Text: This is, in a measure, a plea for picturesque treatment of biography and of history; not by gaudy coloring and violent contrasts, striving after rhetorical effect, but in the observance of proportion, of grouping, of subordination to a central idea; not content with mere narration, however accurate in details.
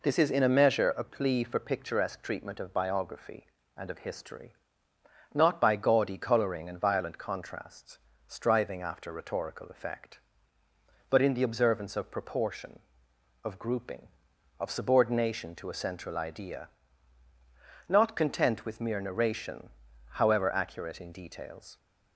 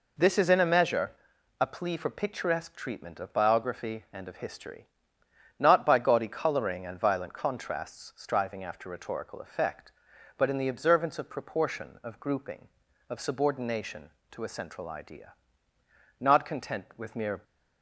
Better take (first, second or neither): first